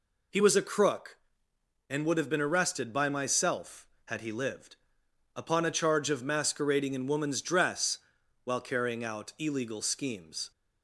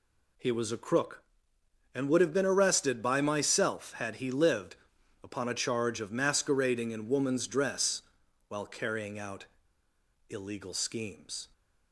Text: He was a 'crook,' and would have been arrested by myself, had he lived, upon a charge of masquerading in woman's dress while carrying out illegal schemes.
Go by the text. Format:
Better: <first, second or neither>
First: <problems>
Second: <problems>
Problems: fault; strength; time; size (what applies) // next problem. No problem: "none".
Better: first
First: pauses between "dress" and "while"; noticeable; at 7.9 s; 0.46 s long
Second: pauses between "dress" and "while"; noticeable; at 8.0 s; 0.48 s long // pauses between "out" and "illegal"; noticeable; at 9.4 s; 0.83 s long